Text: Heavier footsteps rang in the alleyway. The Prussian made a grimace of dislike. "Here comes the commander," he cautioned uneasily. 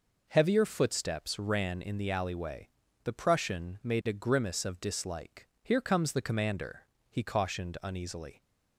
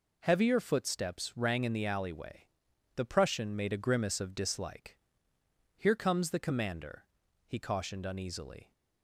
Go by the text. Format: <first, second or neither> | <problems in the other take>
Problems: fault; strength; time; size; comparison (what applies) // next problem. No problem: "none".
second | says "ran" for "rang"; at 1.3 s